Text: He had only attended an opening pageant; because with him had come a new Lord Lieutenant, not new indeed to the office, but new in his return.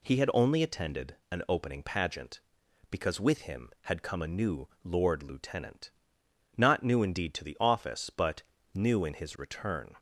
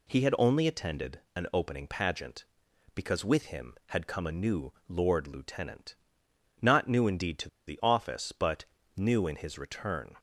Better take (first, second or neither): first